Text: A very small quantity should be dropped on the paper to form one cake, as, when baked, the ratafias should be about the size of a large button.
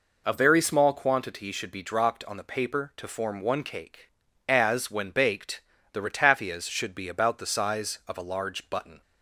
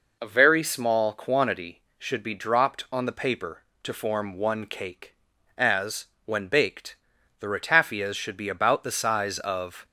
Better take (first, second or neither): first